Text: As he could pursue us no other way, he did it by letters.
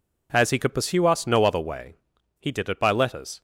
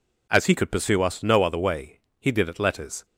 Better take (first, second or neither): first